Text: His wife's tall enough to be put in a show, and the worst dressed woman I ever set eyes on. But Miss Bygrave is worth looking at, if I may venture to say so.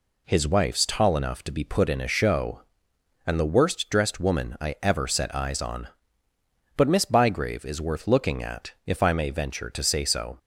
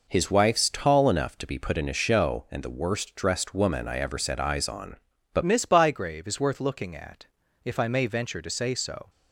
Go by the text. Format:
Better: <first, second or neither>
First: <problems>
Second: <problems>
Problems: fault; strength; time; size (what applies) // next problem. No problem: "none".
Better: first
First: none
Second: changes voice at "Miss"; from 5.4 s on; 3.6 s long